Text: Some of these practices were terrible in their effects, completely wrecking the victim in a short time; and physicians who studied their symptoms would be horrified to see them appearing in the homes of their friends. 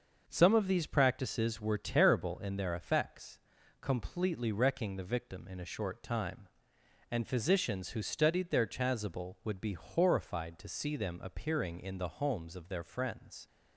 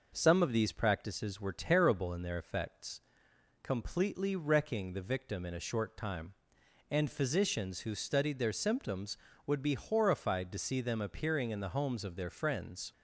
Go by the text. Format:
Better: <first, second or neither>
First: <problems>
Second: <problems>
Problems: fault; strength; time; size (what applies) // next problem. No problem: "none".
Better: second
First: starts louder than the rest; until 1.2 s; 6.5 dB // says "chasuble" for "symptoms"; at 8.6 s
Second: none